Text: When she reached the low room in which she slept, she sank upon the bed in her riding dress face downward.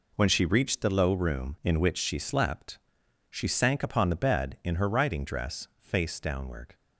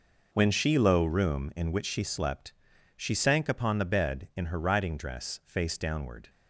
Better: first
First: none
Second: skips "reached the"; at 0.7 s

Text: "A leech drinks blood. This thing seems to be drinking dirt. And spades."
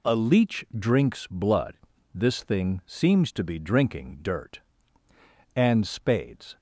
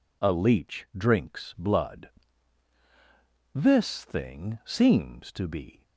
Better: first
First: none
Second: stops before "drinking dirt And spades"; at 5.8 s

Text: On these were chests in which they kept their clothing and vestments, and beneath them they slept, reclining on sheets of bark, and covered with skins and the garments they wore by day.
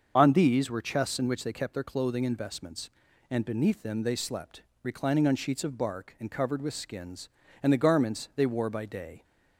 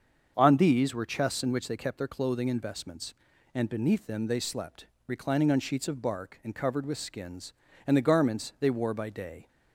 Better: second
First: loses the start of "On"; at 0.1 s; 30 ms // starts louder than the rest; until 1.1 s; 6.5 dB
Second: starts louder than the rest; until 1.3 s; 6.5 dB

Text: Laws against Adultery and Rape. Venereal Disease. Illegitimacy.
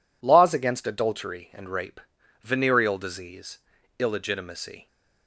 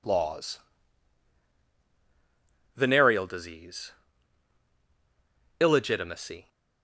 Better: first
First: none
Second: skips "against Adultery and Rape"; at 1.6 s

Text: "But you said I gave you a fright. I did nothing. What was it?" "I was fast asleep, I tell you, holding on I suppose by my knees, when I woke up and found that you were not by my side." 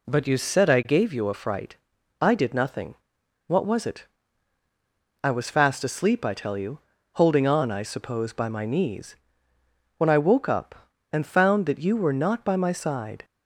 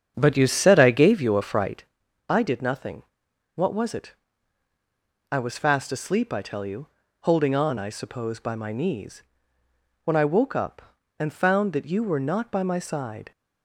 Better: first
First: none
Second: starts louder than the rest; strong; until 1.9 s; 8 dB

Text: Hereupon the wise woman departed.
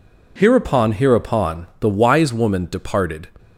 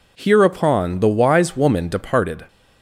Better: second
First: says "Hereupon" twice; at 0.9 s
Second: none

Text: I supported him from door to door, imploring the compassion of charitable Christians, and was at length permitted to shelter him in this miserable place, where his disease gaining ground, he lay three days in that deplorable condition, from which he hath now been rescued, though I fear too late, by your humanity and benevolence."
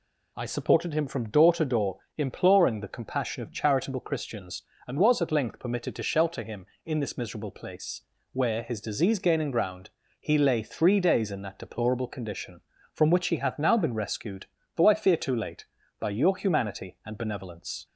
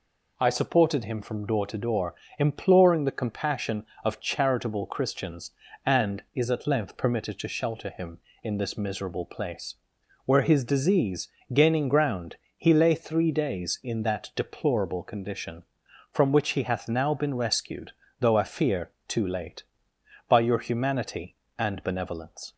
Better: first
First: none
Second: says "is" for "was"; at 6.3 s // pauses between "disease" and "gaining"; slight; at 11.2 s; 0.24 s long // pauses between "fear" and "too"; slight; at 18.8 s; 0.18 s long

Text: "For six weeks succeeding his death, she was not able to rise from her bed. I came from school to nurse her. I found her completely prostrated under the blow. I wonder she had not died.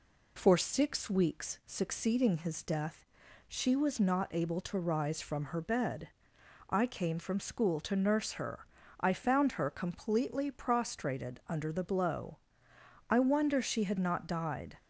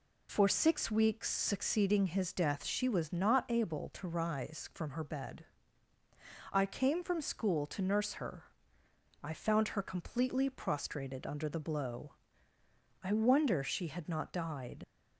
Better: first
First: none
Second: leaves "died" unfinished; at 14.8 s; 75 ms

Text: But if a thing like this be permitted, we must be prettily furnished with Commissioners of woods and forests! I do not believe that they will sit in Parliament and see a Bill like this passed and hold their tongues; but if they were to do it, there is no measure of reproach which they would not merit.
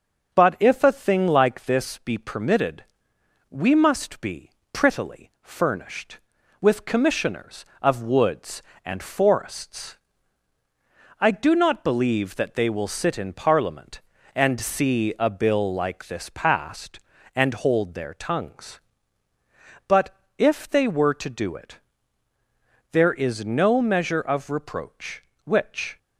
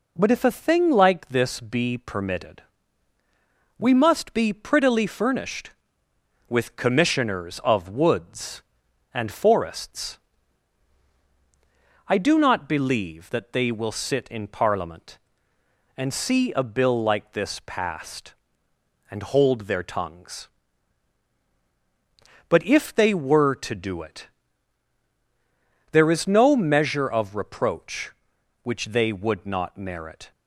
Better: second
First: starts louder than the rest; until 1.3 s; 6.5 dB // pauses between "be" and "prettily"; slight; at 4.4 s; 0.22 s long // pauses between "but" and "if"; slight; at 20.1 s; 0.24 s long // stops before "they would not merit"; at 25.9 s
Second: none

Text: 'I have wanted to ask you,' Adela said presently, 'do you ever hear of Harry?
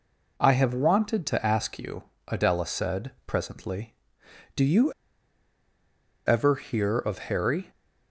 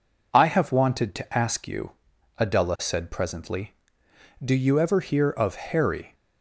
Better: second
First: pauses between "you" and "ever"; strong; at 4.9 s; 1.3 s long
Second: none

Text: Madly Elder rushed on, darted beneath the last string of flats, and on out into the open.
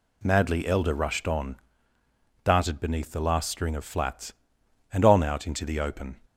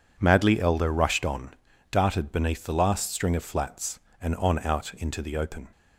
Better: neither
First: none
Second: none

